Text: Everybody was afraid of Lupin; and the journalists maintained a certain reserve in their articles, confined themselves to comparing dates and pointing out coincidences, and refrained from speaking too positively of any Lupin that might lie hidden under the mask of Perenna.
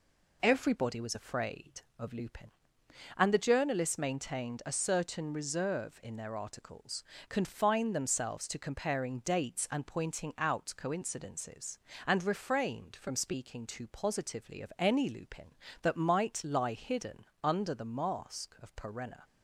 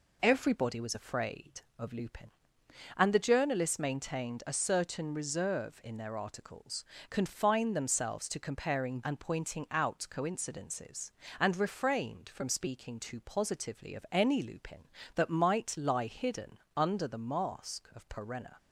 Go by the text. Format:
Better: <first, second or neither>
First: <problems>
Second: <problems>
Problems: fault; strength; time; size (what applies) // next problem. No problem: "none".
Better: first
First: pauses between "hidden" and "under"; slight; at 17.2 s; 0.18 s long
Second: skips "dates"; at 9.0 s // pauses between "hidden" and "under"; slight; at 16.5 s; 0.18 s long